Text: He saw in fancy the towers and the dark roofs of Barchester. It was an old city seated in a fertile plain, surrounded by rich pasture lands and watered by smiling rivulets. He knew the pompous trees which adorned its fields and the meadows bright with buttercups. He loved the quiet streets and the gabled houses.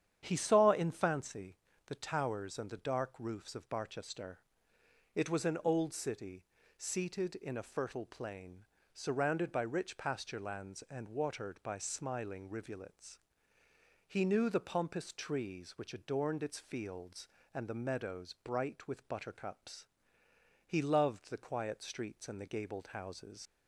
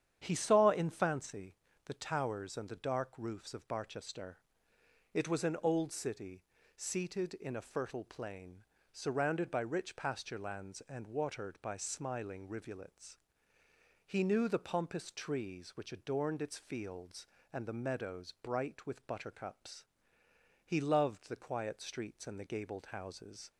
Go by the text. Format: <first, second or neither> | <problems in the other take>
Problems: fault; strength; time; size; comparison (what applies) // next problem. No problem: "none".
second | starts louder than the rest; strong; until 1.2 s; 9 dB; strong in the second // pauses between "fancy" and "the"; slight; at 1.5 s; 0.30 s long; slight in the second // pauses between "city" and "seated"; slight; at 6.4 s; 0.34 s long; slight in the second // leaves "houses" unfinished; at 23.4 s; 65 ms